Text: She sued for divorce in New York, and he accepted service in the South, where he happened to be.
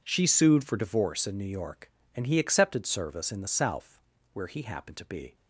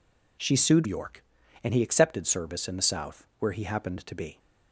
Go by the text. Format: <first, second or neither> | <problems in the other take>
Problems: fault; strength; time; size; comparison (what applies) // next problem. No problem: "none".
first | skips "for divorce in New"; at 0.8 s